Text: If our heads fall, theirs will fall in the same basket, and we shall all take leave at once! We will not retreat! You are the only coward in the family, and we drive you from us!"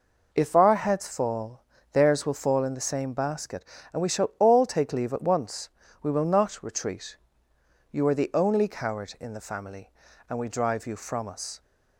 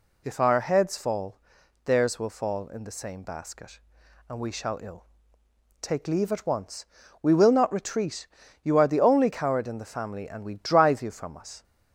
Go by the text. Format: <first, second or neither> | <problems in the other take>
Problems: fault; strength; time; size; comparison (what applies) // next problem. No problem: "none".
first | says "ill" for "all"; at 4.8 s